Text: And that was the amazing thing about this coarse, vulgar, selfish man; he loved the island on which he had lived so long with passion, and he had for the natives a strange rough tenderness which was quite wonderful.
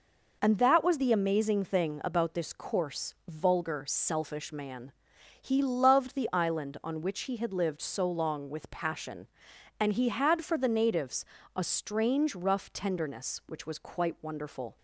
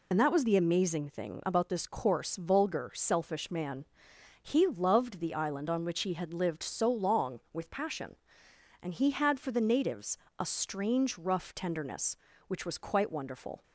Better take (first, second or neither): first